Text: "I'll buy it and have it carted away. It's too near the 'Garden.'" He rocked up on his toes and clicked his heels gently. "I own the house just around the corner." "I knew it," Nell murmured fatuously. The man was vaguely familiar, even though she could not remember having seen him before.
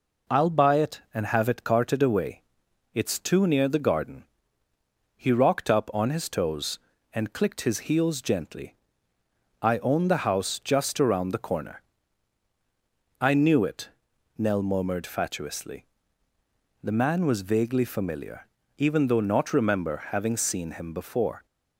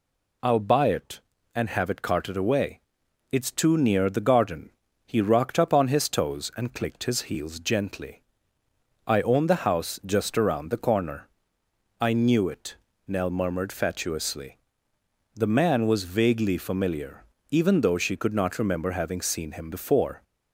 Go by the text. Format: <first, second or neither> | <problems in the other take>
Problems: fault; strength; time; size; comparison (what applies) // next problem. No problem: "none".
second | skips "she could"; at 19.2 s